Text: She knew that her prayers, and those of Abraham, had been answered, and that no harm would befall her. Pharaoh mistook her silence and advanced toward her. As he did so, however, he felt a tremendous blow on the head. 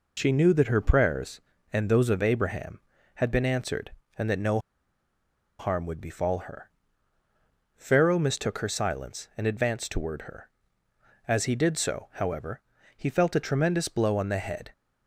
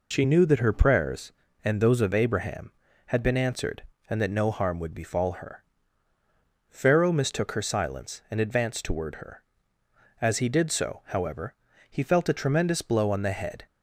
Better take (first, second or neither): second